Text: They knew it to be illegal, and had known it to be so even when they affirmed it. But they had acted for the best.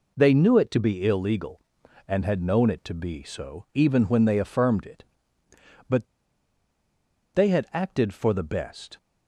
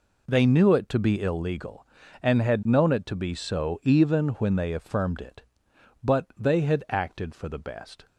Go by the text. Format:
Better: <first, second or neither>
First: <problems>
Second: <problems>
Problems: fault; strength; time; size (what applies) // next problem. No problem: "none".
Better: second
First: pauses between "But" and "they"; strong; at 6.0 s; 1.2 s long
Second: none